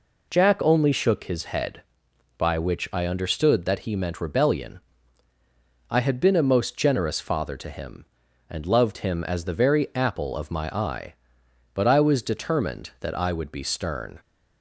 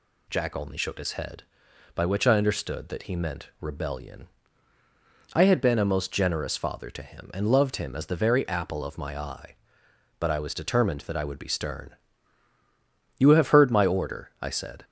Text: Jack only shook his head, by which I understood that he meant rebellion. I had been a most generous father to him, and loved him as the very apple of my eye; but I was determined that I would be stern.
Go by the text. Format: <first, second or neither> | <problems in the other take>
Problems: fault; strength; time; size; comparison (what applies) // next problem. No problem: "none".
first | goes on to say "You have heard my order I said"; strong; from 13.1 s on; 1.6 s long